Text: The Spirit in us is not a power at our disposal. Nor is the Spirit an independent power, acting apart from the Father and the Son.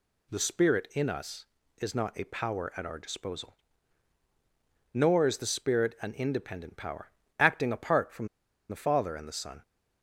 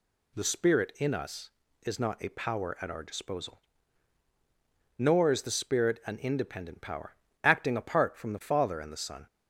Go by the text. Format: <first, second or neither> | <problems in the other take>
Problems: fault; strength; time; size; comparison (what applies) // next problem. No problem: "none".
second | pauses between "from" and "the"; at 8.2 s; 0.42 s long